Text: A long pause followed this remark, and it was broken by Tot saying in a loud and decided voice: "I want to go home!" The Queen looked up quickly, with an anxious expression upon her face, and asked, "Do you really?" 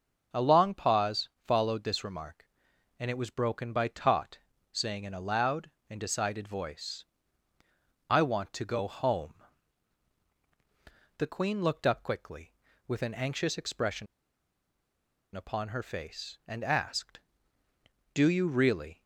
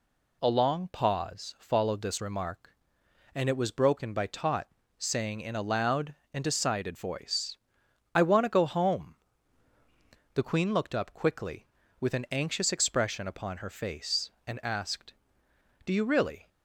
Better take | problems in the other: second | starts louder than the rest; noticeable; until 1.4 s; 6 dB // pauses between "pause" and "followed"; slight; at 1.2 s; 0.16 s long // pauses between "Tot" and "saying"; slight; at 4.3 s; 0.34 s long; slight in the second // pauses between "expression" and "upon"; strong; at 14.0 s; 1.2 s long

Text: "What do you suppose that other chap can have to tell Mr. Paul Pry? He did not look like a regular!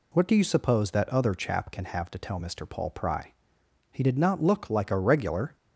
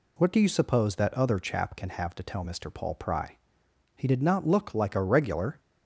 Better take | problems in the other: neither | none

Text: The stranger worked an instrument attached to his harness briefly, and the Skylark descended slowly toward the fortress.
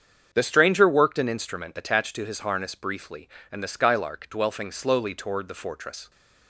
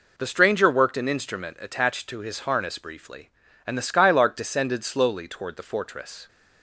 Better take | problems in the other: second | starts louder than the rest; strong; until 1.3 s; 7.5 dB // says "dwelfing" for "descended"; at 4.2 s

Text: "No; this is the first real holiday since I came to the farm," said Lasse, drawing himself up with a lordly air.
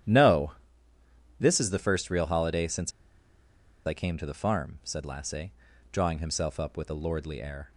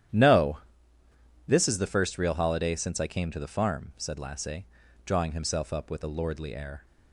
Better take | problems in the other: second | starts louder than the rest; strong; until 1.9 s; 10.5 dB; strong in the second // pauses between "since" and "I"; noticeable; at 2.9 s; 0.94 s long

